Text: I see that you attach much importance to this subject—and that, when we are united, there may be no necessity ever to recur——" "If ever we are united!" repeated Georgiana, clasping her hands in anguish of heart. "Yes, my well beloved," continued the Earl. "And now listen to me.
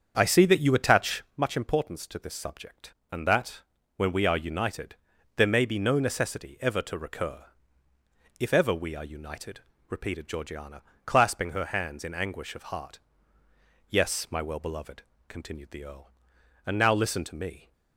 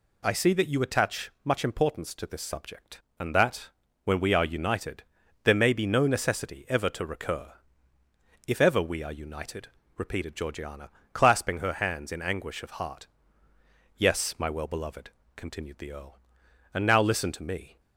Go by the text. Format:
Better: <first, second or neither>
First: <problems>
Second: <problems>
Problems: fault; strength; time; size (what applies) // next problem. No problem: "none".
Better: second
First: starts louder than the rest; strong; until 1.4 s; 7 dB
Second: none